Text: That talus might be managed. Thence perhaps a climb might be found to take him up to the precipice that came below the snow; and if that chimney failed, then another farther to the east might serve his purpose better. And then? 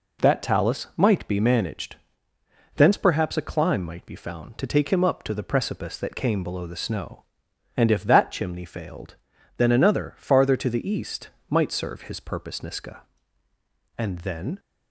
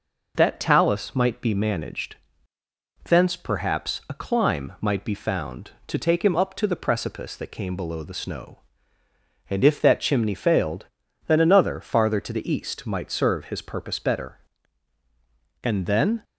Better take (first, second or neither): second